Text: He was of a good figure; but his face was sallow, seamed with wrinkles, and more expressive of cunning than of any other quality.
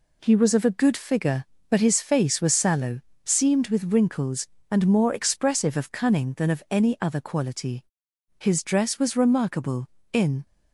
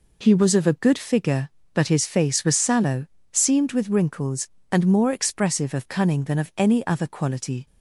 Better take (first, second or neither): second